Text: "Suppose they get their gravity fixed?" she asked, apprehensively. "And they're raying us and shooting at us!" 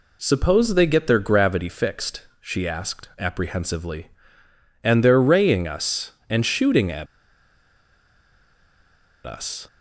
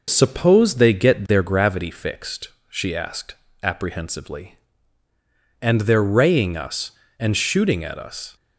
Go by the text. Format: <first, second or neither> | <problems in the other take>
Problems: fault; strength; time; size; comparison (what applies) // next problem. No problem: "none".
second | pauses between "at" and "us"; strong; at 7.0 s; 2.2 s long